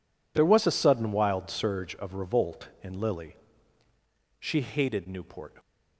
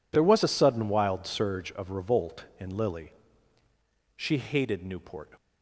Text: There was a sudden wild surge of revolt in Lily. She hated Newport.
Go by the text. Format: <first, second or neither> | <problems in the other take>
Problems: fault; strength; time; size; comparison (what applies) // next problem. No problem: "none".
neither | none